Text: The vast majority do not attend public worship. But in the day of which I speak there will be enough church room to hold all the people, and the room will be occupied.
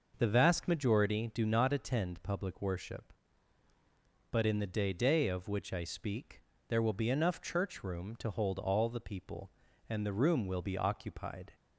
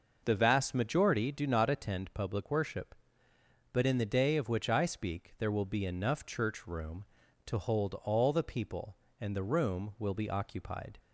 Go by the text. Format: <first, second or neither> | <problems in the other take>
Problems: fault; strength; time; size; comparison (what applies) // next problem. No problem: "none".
second | says "day" twice; at 4.9 s // pauses between "speak" and "there"; slight; at 6.4 s; 0.28 s long